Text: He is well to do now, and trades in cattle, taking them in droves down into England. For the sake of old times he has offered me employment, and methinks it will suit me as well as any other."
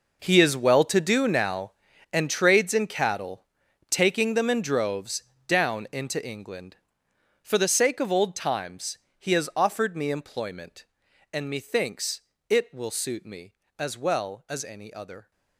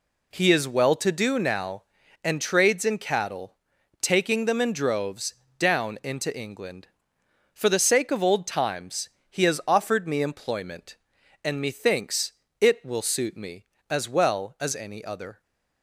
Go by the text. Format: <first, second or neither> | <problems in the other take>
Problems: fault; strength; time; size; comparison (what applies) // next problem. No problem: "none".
second | gets quieter; strong; throughout; 15.5 dB // pauses between "droves" and "down"; slight; at 5.2 s; 0.24 s long; slight in the second // pauses between "times" and "he"; slight; at 8.9 s; 0.20 s long; slight in the second // pauses between "methinks" and "it"; slight; at 12.2 s; 0.30 s long; slight in the second